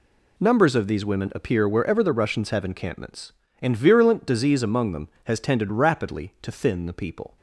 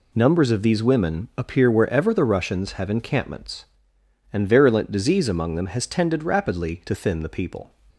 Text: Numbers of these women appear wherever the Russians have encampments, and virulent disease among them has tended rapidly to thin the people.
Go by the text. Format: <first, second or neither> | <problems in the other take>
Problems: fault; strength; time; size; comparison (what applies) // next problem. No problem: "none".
neither | none